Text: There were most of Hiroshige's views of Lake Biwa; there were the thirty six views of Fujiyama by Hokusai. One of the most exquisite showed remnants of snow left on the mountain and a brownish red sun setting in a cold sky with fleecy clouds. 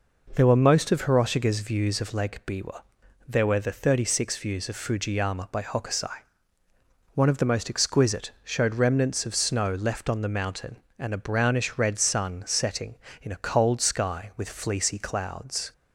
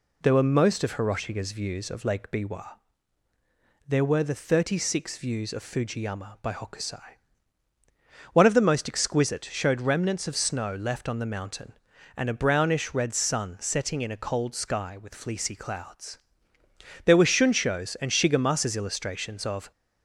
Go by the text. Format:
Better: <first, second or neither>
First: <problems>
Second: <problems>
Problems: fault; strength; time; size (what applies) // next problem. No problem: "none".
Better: first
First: none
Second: goes on to say "There were Shunsho's and Shigemasa's illustrations of"; strong; from 17.0 s on; 2.6 s long